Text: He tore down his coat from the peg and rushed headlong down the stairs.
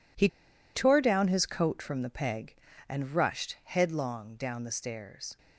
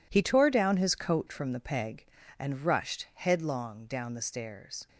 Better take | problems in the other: second | pauses between "He" and "tore"; noticeable; at 0.2 s; 0.46 s long

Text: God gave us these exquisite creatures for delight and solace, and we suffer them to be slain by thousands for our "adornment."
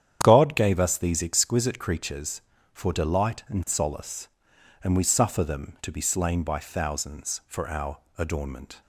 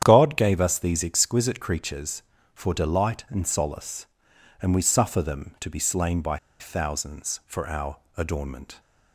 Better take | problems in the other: first | starts louder than the rest; strong; until 1.0 s; 9 dB; strong in the first // pauses between "by" and "thousands"; slight; at 6.3 s; 0.23 s long // pauses between "our" and "adornment"; slight; at 7.9 s; 0.18 s long; slight in the first

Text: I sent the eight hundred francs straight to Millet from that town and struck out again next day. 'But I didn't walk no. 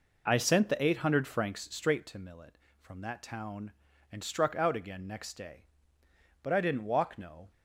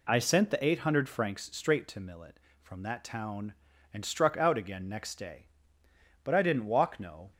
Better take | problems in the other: second | starts louder than the rest; noticeable; until 2.1 s; 4.5 dB

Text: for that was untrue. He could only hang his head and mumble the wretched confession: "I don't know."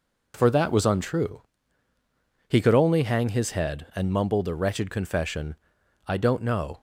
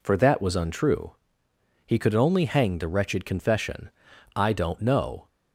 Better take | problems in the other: first | skips "his head and mumble"; at 2.7 s

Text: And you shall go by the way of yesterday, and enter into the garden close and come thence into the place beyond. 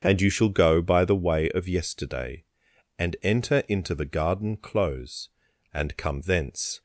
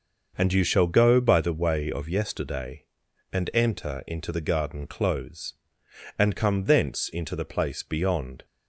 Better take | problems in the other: second | starts louder than the rest; strong; until 1.0 s; 7 dB; noticeable in the second // stops before "into the place beyond"; at 6.7 s

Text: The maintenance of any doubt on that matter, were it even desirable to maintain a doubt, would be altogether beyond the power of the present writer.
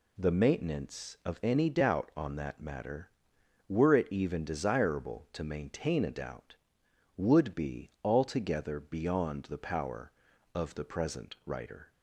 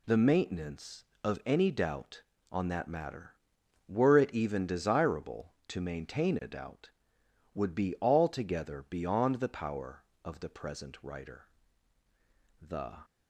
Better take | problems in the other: first | goes on to say "The"; slight; from 12.6 s on; 0.42 s long

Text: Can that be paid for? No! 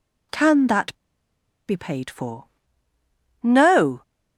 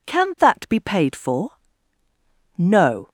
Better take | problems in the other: second | pauses between "that" and "be"; noticeable; at 0.9 s; 0.73 s long

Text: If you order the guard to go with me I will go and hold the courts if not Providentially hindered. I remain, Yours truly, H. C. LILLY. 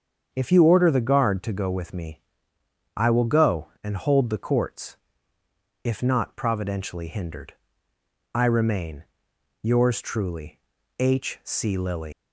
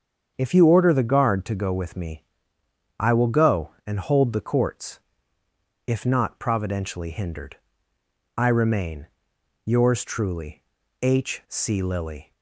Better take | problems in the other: second | starts louder than the rest; strong; until 1.3 s; 7.5 dB; strong in the second // pauses between "me" and "I"; noticeable; at 2.2 s; 0.74 s long; noticeable in the second // pauses between "courts" and "if"; noticeable; at 4.9 s; 0.88 s long; noticeable in the second // leaves "LILLY" unfinished; at 12.1 s; 145 ms

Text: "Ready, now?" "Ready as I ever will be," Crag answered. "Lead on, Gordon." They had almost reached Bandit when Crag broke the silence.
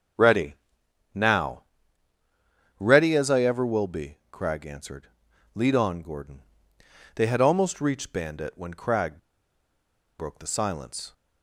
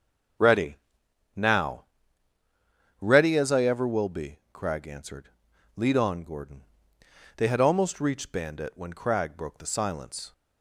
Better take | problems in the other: second | starts louder than the rest; until 2.9 s; 6 dB; also in the second // pauses between "Crag" and "broke"; at 9.1 s; 1.0 s long

